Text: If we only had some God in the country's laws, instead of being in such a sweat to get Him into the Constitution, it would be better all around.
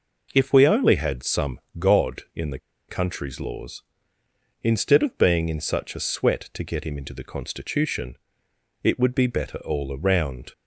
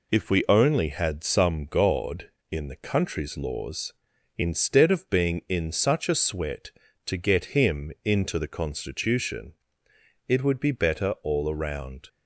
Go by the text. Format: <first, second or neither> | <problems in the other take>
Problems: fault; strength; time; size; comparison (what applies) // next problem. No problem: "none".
second | pauses between "some" and "God"; slight; at 1.5 s; 0.20 s long // pauses between "the" and "country's"; slight; at 2.5 s; 0.31 s long